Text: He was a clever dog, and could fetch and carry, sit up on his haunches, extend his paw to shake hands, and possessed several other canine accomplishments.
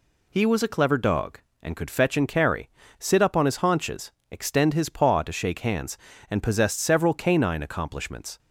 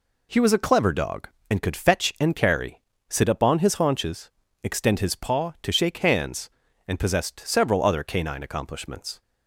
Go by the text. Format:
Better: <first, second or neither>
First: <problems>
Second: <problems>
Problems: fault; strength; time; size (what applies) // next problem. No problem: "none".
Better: second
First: skips "other"; at 7.1 s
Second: none